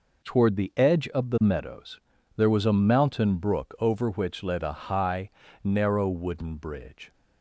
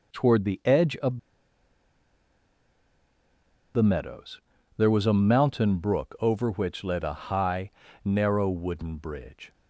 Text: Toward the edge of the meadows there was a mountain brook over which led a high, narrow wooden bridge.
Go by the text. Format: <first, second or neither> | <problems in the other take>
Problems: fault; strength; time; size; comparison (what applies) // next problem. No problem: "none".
first | pauses between "of" and "the"; strong; at 1.1 s; 2.5 s long // pauses between "meadows" and "there"; slight; at 4.4 s; 0.34 s long; slight in the first